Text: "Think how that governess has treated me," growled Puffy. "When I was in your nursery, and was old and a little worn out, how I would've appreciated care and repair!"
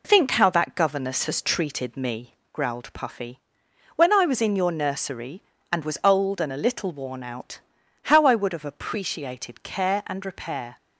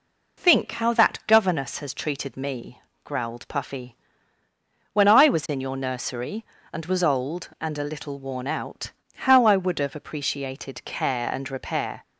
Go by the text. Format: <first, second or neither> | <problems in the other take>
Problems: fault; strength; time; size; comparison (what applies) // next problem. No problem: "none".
neither | none